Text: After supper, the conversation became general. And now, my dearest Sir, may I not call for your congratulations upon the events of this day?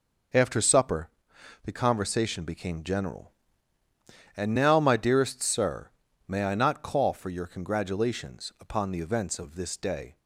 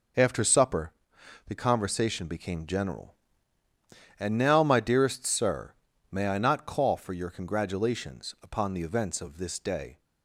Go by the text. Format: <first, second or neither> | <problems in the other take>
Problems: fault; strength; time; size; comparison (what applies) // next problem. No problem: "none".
neither | none